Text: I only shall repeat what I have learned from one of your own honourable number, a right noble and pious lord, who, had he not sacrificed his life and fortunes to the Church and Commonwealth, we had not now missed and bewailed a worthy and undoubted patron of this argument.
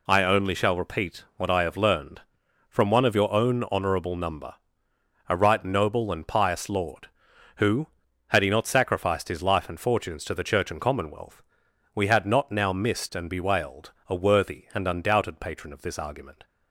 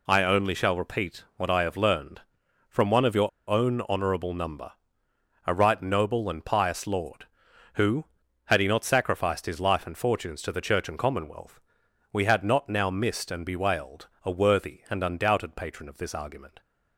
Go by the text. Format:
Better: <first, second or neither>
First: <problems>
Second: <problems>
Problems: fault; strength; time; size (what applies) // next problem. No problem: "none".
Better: first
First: pauses between "bewailed" and "a"; slight; at 13.9 s; 0.16 s long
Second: pauses between "your" and "own"; slight; at 3.2 s; 0.18 s long // pauses between "bewailed" and "a"; slight; at 14.0 s; 0.16 s long